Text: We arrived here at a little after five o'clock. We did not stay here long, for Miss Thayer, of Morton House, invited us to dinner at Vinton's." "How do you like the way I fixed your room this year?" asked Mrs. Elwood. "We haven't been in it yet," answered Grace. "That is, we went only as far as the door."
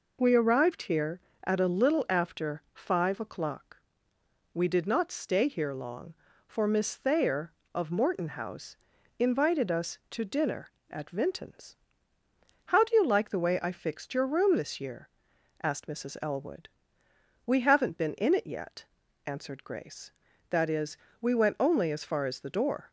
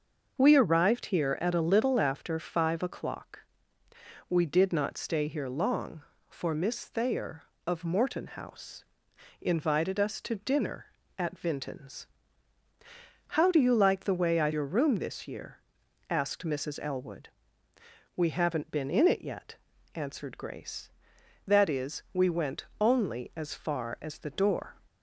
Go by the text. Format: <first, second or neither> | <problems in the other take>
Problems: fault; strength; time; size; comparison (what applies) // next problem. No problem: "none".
first | starts louder than the rest; until 1.3 s; 6 dB // skips "fixed"; at 14.5 s // pauses between "went" and "only"; slight; at 22.6 s; 0.16 s long